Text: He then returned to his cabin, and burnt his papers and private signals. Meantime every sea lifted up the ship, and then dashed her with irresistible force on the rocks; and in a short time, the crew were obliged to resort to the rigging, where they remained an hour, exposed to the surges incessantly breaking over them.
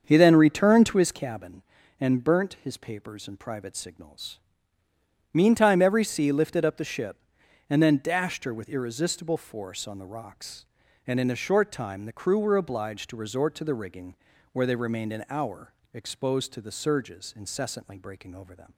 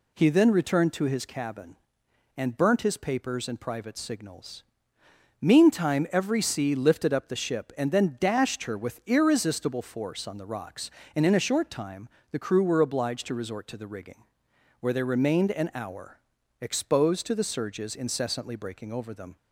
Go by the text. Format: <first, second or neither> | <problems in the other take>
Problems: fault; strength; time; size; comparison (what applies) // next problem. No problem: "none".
second | starts louder than the rest; until 1.8 s; 7 dB